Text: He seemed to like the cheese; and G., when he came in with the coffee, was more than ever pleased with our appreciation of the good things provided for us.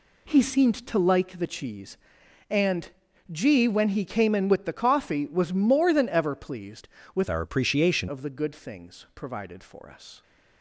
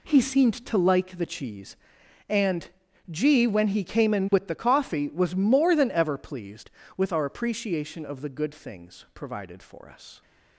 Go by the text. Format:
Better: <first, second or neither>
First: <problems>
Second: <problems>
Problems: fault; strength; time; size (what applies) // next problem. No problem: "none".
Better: second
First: pauses between "and" and "G"; at 2.9 s; 0.40 s long // changes voice from "our" to "appreciation"; from 7.2 to 8.0 s; 0.8 s long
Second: pauses between "and" and "G"; at 2.6 s; 0.40 s long